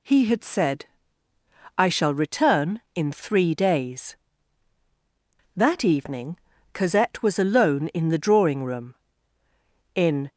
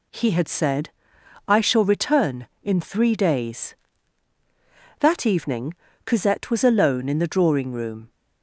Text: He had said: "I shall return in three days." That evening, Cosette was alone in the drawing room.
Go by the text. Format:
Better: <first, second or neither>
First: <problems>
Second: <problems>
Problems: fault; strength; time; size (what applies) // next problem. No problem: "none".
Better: second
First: goes on to say "In"; slight; from 9.9 s on; 0.34 s long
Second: none